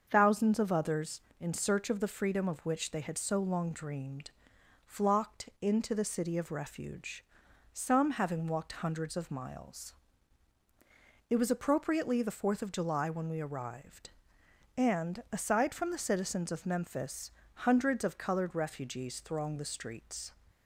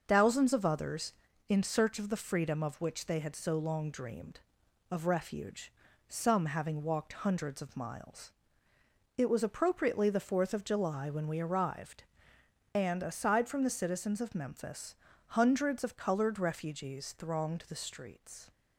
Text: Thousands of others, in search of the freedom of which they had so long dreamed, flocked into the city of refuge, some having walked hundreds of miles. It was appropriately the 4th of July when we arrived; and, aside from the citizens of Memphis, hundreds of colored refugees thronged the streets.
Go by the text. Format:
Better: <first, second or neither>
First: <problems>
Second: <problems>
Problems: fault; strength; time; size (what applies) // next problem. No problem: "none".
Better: first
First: starts louder than the rest; until 1.1 s; 6.5 dB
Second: starts louder than the rest; until 1.0 s; 6 dB // skips "flocked into the city"; at 4.6 s